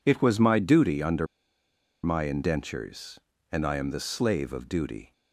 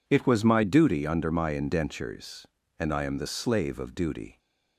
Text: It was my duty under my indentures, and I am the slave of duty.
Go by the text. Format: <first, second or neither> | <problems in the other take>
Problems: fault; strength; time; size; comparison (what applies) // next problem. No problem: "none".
second | pauses between "under" and "my"; noticeable; at 1.2 s; 0.77 s long